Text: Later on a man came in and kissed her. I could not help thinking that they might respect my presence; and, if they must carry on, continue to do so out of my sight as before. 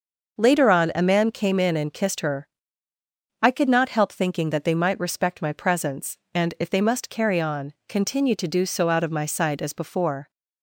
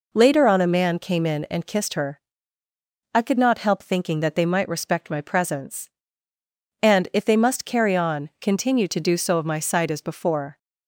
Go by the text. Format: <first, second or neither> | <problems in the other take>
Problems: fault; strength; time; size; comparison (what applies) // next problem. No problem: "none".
first | skips "out"; at 9.3 s